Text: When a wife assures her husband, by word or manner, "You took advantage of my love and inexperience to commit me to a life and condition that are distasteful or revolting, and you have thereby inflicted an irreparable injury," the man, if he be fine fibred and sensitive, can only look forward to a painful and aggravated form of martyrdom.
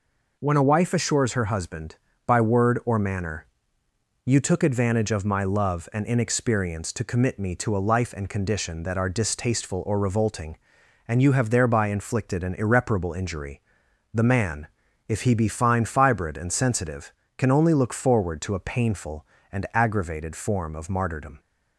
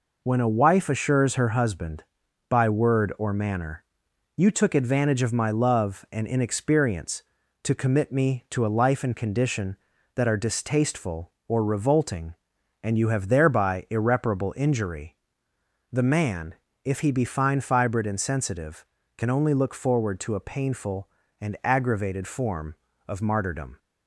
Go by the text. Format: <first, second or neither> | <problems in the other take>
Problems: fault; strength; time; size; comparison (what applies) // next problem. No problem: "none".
first | skips "inflicted an"; at 13.8 s